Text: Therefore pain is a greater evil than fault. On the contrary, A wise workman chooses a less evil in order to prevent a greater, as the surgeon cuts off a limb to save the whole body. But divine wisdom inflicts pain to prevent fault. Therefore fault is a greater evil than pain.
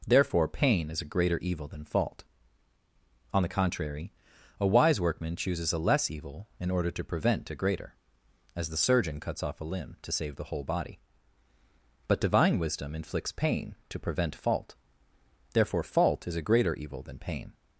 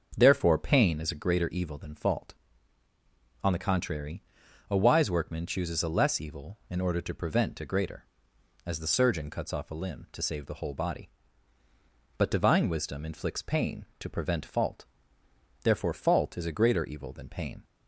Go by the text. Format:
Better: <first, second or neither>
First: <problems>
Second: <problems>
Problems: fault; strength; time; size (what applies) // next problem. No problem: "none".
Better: first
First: none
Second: starts louder than the rest; until 1.3 s; 6 dB